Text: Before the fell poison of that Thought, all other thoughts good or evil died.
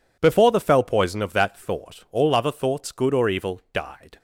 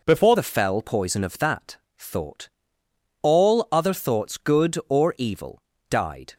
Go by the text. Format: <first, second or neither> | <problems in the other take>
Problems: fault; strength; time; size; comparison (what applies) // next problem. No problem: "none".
first | changes voice at "the"; from 0.3 s on; 6.0 s long // pauses between "that" and "Thought"; slight; at 1.7 s; 0.22 s long // pauses between "evil" and "died"; slight; at 5.6 s; 0.28 s long